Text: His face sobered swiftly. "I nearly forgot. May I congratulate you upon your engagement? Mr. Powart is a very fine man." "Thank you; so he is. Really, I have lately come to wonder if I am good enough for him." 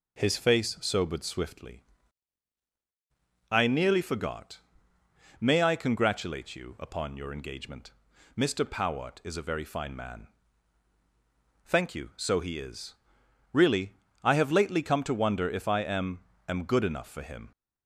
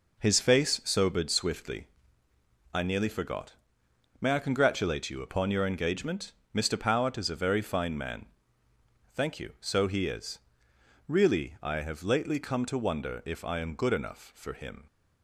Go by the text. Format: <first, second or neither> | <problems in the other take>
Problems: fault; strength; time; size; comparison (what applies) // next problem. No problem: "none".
second | says "am" twice; at 16.4 s